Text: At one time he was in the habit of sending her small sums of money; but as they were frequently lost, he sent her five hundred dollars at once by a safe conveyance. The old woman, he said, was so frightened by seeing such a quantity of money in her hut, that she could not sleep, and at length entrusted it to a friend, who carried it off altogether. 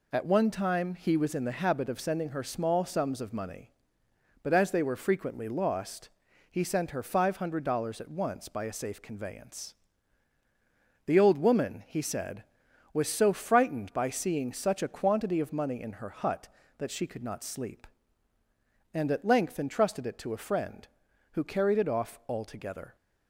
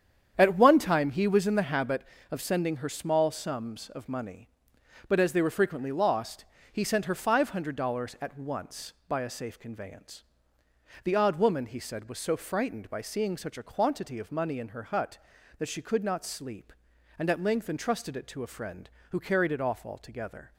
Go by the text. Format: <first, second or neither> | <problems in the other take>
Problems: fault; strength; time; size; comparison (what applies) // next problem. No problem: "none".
first | starts louder than the rest; strong; until 1.3 s; 8.5 dB // says "odd" for "old"; at 11.1 s